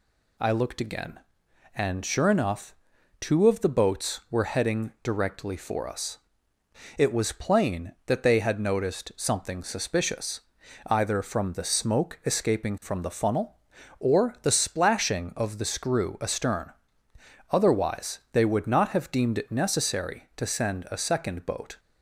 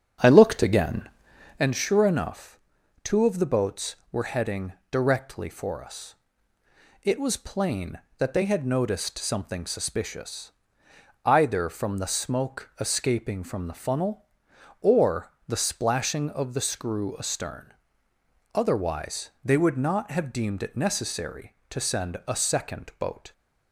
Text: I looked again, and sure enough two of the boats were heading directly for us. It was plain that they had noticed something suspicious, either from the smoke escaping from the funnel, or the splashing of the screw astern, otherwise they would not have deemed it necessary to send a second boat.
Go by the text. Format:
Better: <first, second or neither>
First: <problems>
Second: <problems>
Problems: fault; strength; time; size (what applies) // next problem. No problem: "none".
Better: first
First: pauses between "enough" and "two"; noticeable; at 2.7 s; 0.46 s long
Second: starts louder than the rest; strong; until 1.6 s; 8 dB // pauses between "enough" and "two"; noticeable; at 2.5 s; 0.46 s long // pauses between "heading" and "directly"; slight; at 4.7 s; 0.16 s long // pauses between "or" and "the"; slight; at 15.3 s; 0.16 s long